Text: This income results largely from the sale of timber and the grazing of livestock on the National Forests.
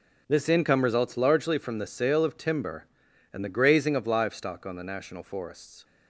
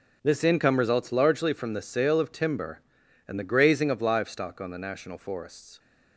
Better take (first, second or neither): neither